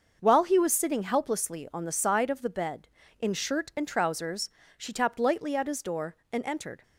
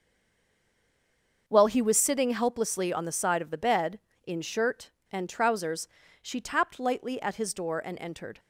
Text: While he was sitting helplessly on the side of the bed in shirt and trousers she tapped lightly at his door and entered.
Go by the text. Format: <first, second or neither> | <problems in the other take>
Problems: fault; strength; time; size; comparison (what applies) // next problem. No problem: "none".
first | stays silent before the first word; noticeable; until 1.4 s; 1.4 s long // starts louder than the rest; until 2.4 s; 6.5 dB; also in the first // pauses between "trousers" and "she"; slight; at 5.8 s; 0.34 s long; slight in the first